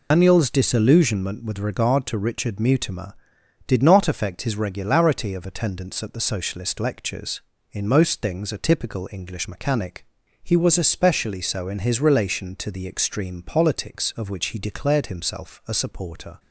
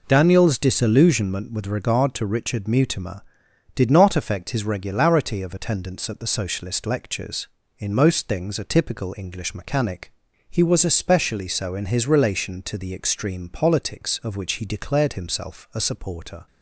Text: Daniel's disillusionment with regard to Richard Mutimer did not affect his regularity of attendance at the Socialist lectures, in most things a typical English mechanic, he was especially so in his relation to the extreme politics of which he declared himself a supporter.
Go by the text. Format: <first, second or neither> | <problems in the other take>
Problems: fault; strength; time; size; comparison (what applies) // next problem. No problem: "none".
second | loses the start of "Daniel's"; at 0.1 s; 145 ms